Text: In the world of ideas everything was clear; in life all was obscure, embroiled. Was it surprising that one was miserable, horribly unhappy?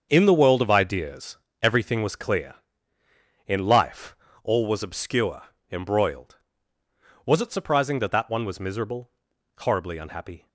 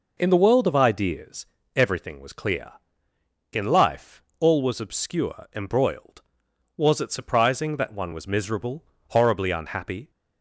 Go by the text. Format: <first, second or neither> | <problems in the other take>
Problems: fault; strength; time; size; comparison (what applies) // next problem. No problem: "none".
second | starts louder than the rest; until 1.1 s; 6.5 dB // pauses between "ideas" and "everything"; slight; at 1.3 s; 0.24 s long; slight in the second // pauses between "life" and "all"; slight; at 4.1 s; 0.26 s long; slight in the second // says "that" twice; at 8.1 s